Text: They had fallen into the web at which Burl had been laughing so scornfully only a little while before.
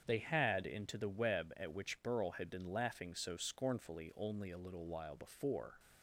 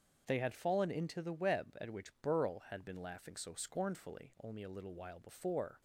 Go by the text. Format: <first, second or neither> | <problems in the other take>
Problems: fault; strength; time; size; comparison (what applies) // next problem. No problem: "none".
second | starts louder than the rest; strong; until 1.0 s; 7.5 dB; also in the second // skips "fallen"; at 0.6 s